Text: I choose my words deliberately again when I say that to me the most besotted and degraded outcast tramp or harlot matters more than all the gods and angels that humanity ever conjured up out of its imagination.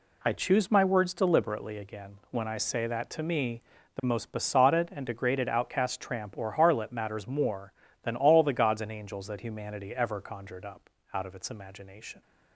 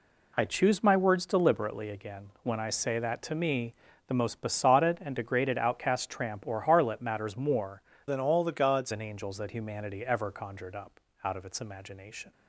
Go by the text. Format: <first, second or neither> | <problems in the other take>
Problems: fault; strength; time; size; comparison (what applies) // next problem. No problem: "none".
first | pauses between "again" and "when"; slight; at 2.2 s; 0.16 s long; slight in the first // pauses between "me" and "the"; slight; at 3.7 s; 0.36 s long; slight in the first // changes voice from "than" to "gods"; from 8.0 to 8.9 s; 0.9 s long // pauses between "up" and "out"; slight; at 10.9 s; 0.24 s long; slight in the first